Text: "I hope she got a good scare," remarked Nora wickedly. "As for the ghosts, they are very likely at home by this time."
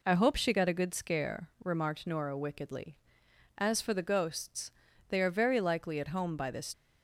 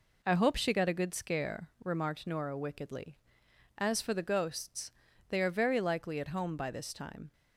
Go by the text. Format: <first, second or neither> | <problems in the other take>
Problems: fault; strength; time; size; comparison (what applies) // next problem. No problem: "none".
second | stops before "time"; at 6.7 s